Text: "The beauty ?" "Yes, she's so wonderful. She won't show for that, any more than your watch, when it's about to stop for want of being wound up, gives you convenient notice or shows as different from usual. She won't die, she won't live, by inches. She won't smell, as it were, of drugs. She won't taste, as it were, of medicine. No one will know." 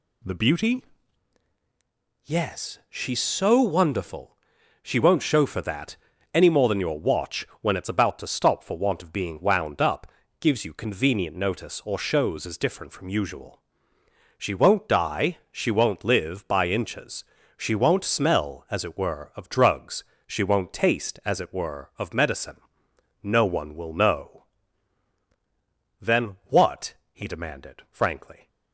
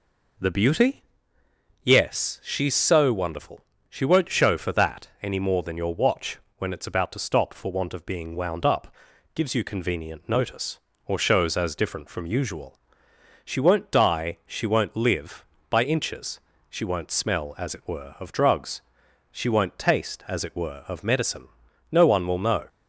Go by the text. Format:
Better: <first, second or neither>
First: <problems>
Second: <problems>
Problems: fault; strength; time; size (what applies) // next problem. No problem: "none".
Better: second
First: goes on to say "Then what he demanded frankly"; strong; from 25.9 s on; 2.4 s long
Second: none